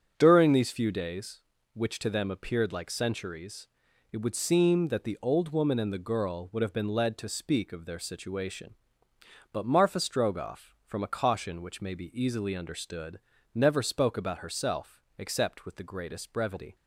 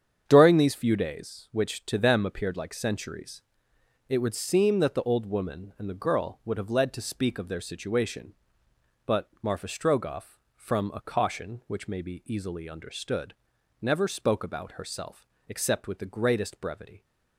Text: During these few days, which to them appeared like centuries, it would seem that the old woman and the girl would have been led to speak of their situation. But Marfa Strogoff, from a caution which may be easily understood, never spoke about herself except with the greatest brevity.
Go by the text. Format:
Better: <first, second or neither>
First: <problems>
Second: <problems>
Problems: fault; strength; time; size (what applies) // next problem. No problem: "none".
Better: first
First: starts louder than the rest; until 1.1 s; 7 dB // pauses between "herself" and "except"; slight; at 15.0 s; 0.18 s long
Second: starts louder than the rest; strong; until 1.2 s; 8 dB // skips "been"; at 6.6 s // pauses between "herself" and "except"; slight; at 15.2 s; 0.22 s long